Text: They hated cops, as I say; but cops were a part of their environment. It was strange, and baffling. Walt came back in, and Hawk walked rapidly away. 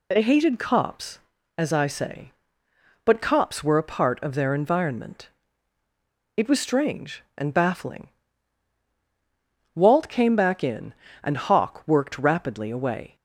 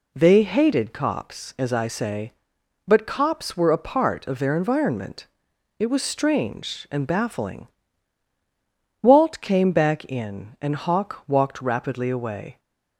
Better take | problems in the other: second | says "worked" for "walked"; at 11.8 s

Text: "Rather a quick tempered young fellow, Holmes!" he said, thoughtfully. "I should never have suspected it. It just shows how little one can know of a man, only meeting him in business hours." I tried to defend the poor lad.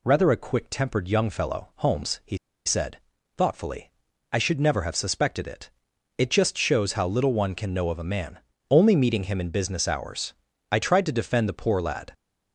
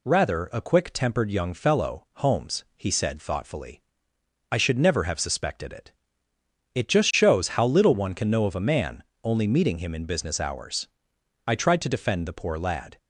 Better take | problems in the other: second | pauses between "he" and "said"; slight; at 2.3 s; 0.28 s long

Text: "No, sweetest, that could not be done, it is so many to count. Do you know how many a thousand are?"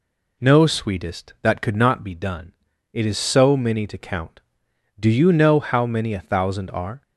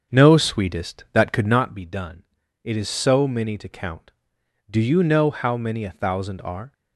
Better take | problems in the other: first | starts louder than the rest; strong; until 1.6 s; 7 dB

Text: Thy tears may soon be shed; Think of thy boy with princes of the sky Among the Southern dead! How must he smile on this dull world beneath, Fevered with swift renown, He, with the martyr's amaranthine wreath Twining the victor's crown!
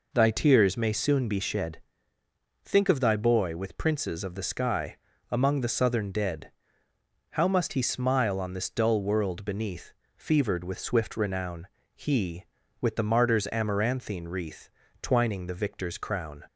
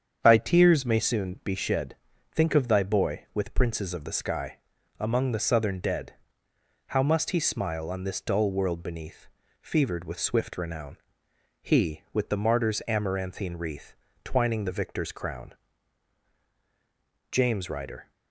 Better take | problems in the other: first | starts louder than the rest; strong; until 1.2 s; 8 dB // pauses between "sky" and "Among"; at 4.5 s; 0.40 s long; slight in the first // pauses between "wreath" and "Twining"; slight; at 13.9 s; 0.28 s long; slight in the first // goes on to say "JAMES RYDER"; noticeable; from 17.3 s on; 0.80 s long

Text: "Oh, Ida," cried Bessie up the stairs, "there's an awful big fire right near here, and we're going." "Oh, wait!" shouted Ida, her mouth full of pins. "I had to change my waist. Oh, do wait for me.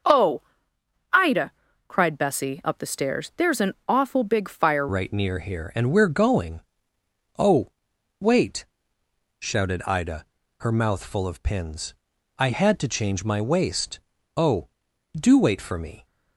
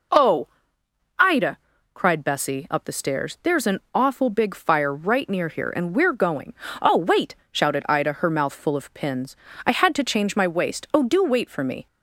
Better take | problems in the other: second | starts louder than the rest; until 2.1 s; 6.5 dB // changes voice at "right"; from 4.8 s on; 11.2 s long

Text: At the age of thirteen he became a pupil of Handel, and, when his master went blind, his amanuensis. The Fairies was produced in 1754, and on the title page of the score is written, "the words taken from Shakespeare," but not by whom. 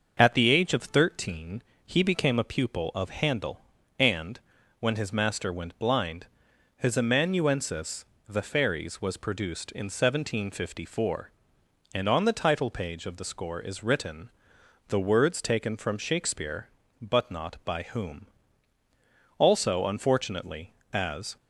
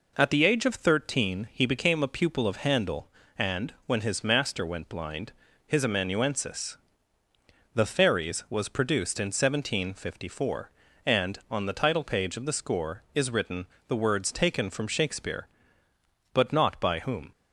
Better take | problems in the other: second | starts louder than the rest; until 1.1 s; 6.5 dB // pauses between "thirteen" and "he"; slight; at 1.6 s; 0.24 s long // goes on to say "Also unfortunately as"; strong; from 19.3 s on; 1.9 s long

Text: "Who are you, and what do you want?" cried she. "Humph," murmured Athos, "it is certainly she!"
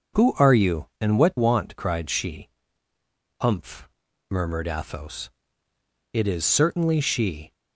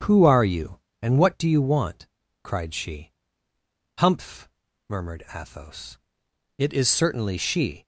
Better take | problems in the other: second | starts louder than the rest; noticeable; until 1.3 s; 6 dB; strong in the second // skips "do you"; at 1.3 s

